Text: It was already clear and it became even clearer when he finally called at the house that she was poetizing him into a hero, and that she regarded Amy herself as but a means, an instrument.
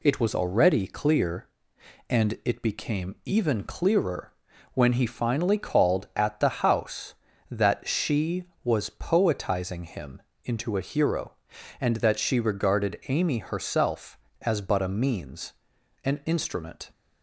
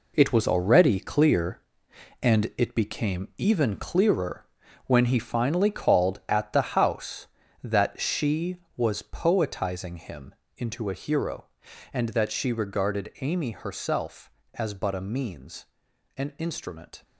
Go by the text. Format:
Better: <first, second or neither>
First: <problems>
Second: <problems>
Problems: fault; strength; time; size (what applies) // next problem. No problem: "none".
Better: first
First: pauses between "clearer" and "when"; at 4.3 s; 0.42 s long // pauses between "him" and "into"; slight; at 10.2 s; 0.22 s long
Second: gets quieter; strong; throughout; 9.5 dB // pauses between "clearer" and "when"; at 4.4 s; 0.42 s long // pauses between "him" and "into"; slight; at 10.3 s; 0.22 s long